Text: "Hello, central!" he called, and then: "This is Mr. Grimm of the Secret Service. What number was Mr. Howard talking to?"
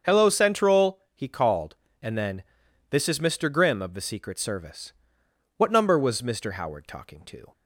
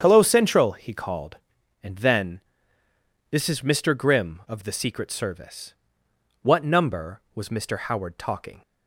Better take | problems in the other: first | starts louder than the rest; strong; until 1.0 s; 7.5 dB; also in the first // stops before "to"; at 8.6 s

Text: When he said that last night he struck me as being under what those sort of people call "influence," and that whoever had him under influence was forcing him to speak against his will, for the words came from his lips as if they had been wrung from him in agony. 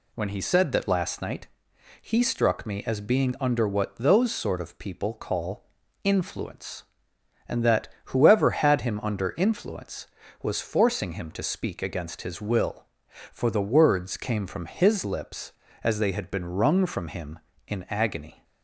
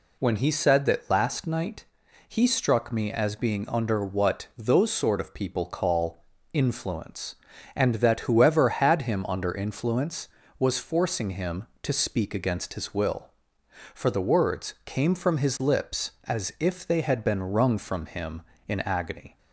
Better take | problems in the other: second | pauses between "night" and "he"; noticeable; at 1.4 s; 0.56 s long; also in the second // pauses between "call" and "influence"; at 5.6 s; 0.38 s long; slight in the second // pauses between "that" and "whoever"; slight; at 7.8 s; 0.20 s long // skips "if"; at 15.9 s

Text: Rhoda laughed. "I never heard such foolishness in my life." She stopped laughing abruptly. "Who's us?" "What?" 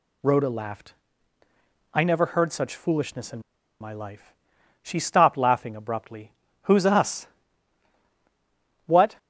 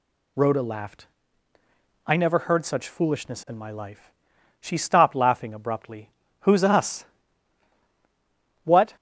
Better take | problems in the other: second | pauses between "in" and "my"; at 3.3 s; 0.41 s long

